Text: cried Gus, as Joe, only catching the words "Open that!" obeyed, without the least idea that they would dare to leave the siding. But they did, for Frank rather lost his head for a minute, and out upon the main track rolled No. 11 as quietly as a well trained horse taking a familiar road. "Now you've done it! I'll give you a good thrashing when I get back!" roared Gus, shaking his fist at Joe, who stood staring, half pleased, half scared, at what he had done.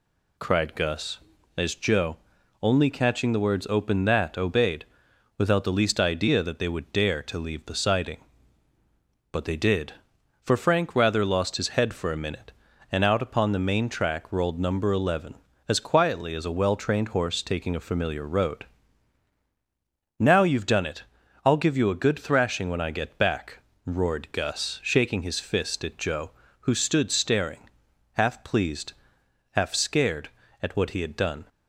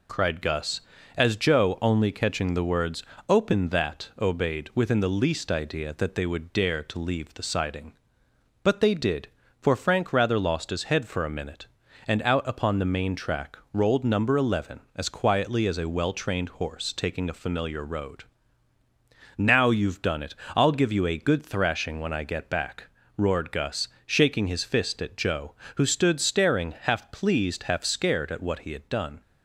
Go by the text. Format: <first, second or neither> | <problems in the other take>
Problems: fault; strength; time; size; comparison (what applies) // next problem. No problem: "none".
first | pauses between "words" and "Open"; slight; at 3.0 s; 0.24 s long // says "within" for "without"; at 4.7 s // pauses between "track" and "rolled"; slight; at 13.5 s; 0.16 s long